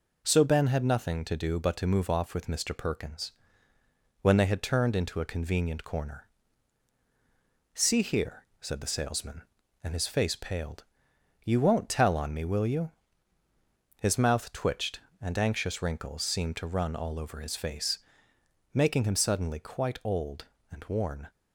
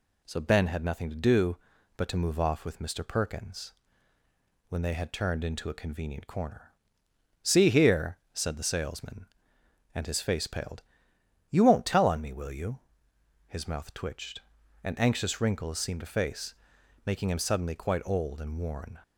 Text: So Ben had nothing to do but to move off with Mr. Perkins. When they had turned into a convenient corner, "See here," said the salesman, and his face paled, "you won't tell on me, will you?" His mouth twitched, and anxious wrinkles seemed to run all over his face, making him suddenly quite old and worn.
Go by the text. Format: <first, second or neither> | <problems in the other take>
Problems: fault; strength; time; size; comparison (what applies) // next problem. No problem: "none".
first | skips "run all over his"; at 16.0 s